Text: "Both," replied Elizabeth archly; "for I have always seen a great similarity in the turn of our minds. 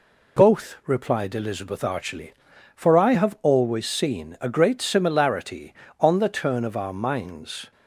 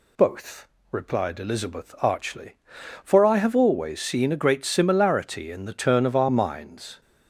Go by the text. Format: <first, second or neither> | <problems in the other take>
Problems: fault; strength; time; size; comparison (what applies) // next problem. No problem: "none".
second | says "on" for "in"; at 5.9 s